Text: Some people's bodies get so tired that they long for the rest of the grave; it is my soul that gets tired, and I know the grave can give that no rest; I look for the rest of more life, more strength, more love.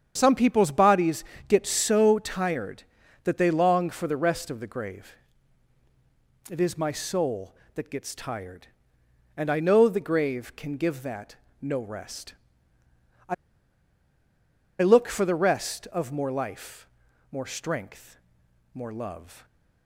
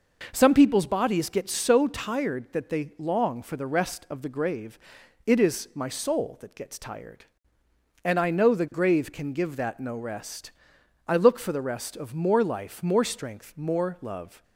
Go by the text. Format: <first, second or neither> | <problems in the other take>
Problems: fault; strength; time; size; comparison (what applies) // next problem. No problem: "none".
second | starts louder than the rest; strong; until 1.1 s; 8 dB // pauses between "bodies" and "get"; slight; at 1.2 s; 0.22 s long // pauses between "that" and "no"; slight; at 11.3 s; 0.24 s long // pauses between "I" and "look"; strong; at 13.3 s; 1.4 s long